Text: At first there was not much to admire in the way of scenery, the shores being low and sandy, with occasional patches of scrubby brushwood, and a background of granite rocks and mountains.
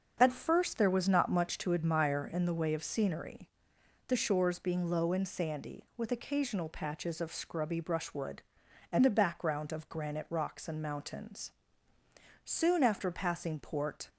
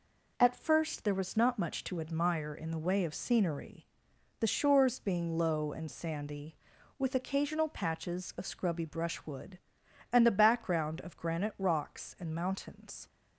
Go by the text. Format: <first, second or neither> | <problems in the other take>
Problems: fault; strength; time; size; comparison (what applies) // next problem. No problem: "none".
second | starts louder than the rest; until 1.2 s; 6.5 dB // goes on to say "Soon after passing Port"; from 12.4 s on; 1.6 s long